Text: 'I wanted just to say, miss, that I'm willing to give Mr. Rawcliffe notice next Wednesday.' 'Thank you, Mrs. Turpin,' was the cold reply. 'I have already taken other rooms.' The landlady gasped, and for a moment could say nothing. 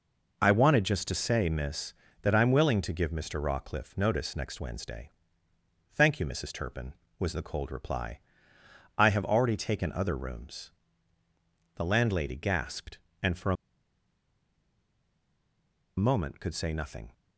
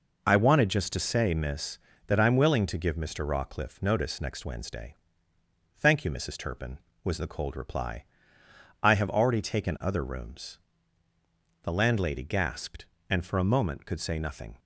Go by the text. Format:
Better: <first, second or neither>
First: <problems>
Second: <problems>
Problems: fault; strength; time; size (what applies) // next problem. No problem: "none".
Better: second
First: pauses between "a" and "moment"; strong; at 13.5 s; 2.4 s long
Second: none